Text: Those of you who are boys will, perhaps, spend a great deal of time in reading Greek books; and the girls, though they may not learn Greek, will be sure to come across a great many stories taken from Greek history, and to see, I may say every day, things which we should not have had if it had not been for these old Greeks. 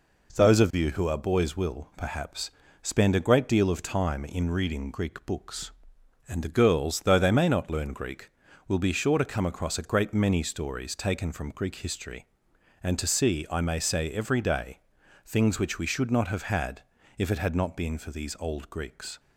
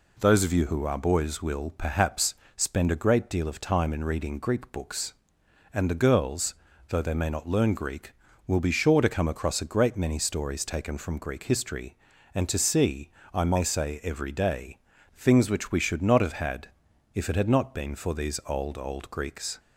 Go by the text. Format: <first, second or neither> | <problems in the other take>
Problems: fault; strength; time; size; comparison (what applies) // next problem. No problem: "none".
first | pauses between "had" and "if"; at 16.6 s; 0.44 s long; also in the first // says "old" twice; at 18.7 s